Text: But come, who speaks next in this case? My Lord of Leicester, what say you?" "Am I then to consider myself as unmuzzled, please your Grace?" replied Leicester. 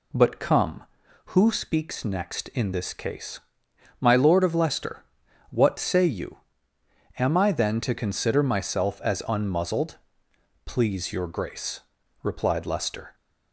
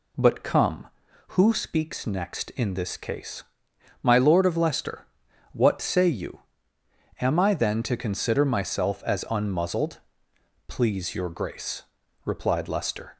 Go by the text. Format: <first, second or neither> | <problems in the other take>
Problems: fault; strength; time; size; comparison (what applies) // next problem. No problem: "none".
neither | none